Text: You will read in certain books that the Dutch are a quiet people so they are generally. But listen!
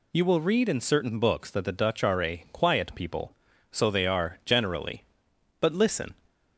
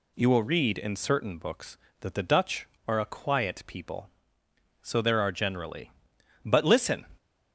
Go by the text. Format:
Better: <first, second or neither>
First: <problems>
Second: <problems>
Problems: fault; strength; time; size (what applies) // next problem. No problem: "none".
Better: first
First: none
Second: says "there" for "they"; at 4.9 s